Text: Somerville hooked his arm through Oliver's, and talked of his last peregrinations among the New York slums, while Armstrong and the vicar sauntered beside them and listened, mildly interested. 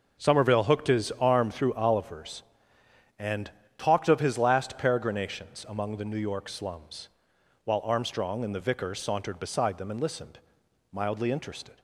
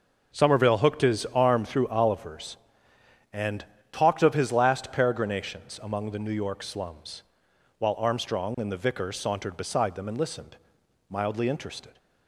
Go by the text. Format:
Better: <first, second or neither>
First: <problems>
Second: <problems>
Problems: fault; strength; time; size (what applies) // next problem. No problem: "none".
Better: neither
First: starts louder than the rest; until 1.2 s; 6.5 dB // pauses between "and" and "talked"; slight; at 3.5 s; 0.24 s long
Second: starts louder than the rest; until 1.4 s; 6.5 dB // pauses between "and" and "talked"; slight; at 3.6 s; 0.24 s long